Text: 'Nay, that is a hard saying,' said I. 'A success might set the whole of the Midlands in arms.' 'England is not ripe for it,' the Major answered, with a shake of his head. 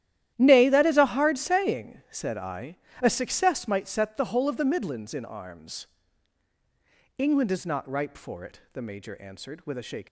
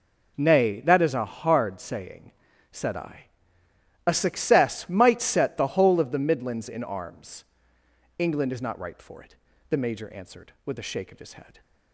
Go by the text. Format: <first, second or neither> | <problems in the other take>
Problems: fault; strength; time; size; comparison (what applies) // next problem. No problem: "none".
second | starts louder than the rest; strong; until 1.3 s; 12 dB // stops before "of his head"; at 10.0 s